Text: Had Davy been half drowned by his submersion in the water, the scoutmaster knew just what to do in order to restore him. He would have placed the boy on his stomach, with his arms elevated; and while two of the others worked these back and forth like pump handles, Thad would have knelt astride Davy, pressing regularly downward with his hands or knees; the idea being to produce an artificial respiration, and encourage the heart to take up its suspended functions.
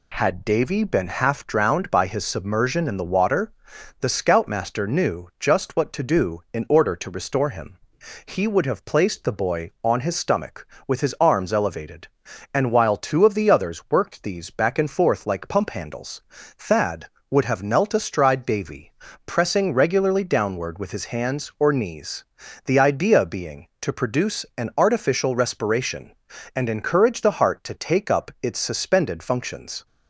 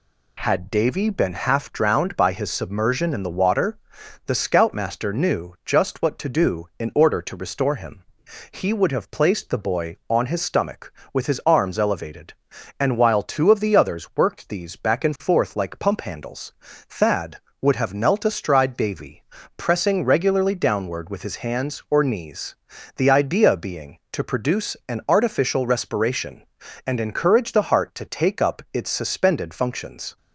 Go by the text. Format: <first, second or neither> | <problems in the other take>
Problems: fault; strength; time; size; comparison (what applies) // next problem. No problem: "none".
neither | none